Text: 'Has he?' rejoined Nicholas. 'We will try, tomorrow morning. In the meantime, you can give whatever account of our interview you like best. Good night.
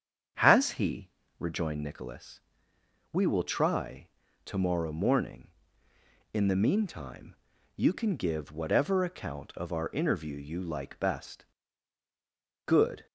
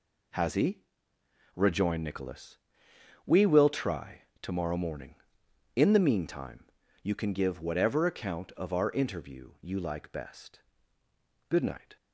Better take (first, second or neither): second